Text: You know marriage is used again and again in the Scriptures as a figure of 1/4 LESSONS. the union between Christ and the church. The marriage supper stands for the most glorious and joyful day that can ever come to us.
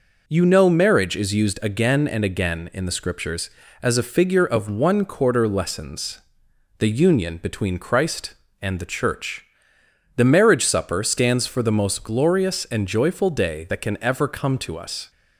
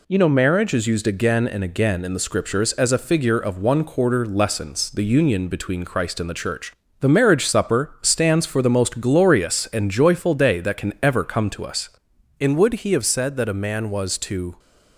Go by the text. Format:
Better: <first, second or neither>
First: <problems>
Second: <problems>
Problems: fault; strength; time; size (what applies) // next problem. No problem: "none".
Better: first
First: none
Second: goes on to say "And would he have said that a man was to"; strong; from 12.3 s on; 2.1 s long